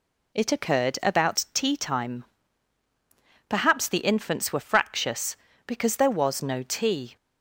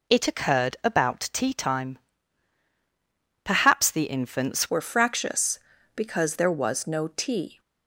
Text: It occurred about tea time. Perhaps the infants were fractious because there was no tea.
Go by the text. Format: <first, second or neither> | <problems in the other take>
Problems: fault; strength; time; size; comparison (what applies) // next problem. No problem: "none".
first | changes voice at "were"; from 4.6 s on; 2.9 s long